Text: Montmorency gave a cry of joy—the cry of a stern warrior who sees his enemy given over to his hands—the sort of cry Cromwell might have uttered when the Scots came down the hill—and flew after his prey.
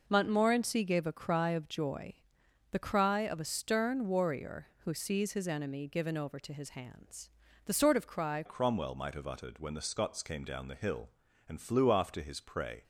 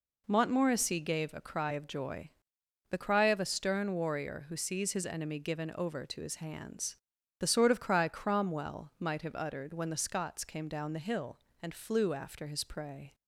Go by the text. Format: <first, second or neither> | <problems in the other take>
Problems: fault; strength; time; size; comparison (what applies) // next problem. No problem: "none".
second | changes voice at "Cromwell"; from 8.4 s on; 4.4 s long